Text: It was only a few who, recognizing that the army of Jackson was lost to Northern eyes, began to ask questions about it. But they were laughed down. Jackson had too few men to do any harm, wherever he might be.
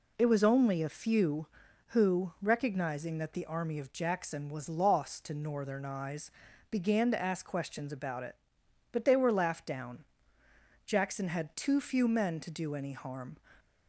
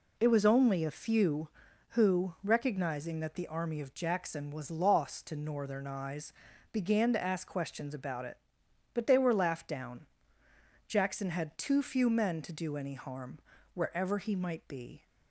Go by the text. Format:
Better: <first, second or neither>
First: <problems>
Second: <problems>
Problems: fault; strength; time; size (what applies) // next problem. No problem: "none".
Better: second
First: stops before "wherever he might be"; at 13.5 s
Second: none